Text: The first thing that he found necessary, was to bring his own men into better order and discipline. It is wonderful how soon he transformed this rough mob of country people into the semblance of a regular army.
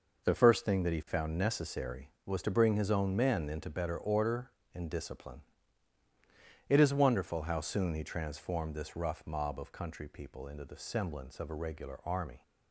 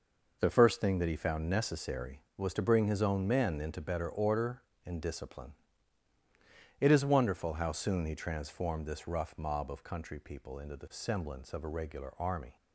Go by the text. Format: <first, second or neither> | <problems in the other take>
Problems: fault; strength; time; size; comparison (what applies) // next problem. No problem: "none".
neither | none